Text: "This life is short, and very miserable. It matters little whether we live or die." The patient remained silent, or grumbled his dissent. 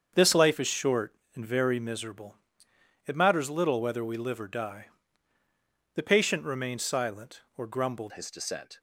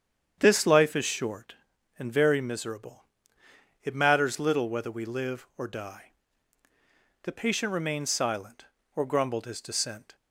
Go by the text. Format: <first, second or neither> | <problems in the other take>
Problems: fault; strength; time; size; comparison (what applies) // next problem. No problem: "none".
second | starts louder than the rest; until 1.1 s; 7 dB; strong in the second // changes voice at "his"; from 8.1 s on; 0.6 s long